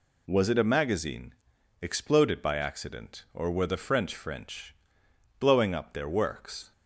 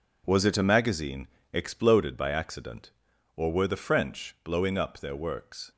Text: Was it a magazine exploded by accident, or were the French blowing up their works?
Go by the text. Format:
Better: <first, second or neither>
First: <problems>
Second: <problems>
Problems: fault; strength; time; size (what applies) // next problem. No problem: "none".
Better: second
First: pauses between "magazine" and "exploded"; noticeable; at 1.3 s; 0.48 s long // says "French" twice; at 4.1 s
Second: pauses between "magazine" and "exploded"; slight; at 1.2 s; 0.26 s long